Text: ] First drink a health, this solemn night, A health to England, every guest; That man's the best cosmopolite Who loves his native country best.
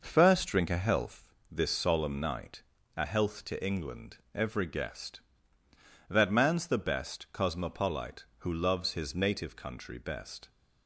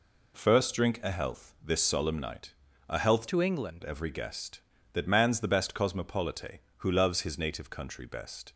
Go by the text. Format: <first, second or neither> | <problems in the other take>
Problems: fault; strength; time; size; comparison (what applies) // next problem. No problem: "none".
first | changes voice from "to" to "England"; from 3.2 to 3.8 s; 0.6 s long